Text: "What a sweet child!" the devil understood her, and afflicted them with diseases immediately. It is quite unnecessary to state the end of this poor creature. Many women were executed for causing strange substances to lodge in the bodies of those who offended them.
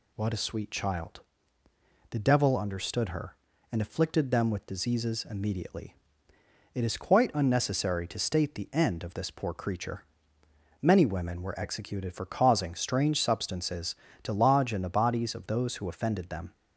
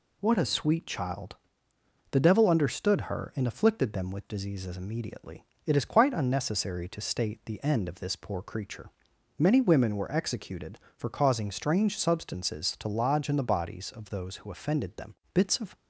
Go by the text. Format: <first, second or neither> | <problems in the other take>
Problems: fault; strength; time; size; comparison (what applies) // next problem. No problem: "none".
first | goes on to say "Bits of"; slight; from 15.3 s on; 0.42 s long